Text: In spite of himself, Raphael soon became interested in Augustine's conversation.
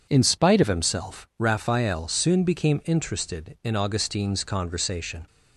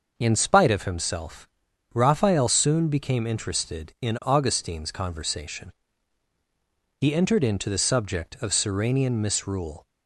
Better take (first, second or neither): first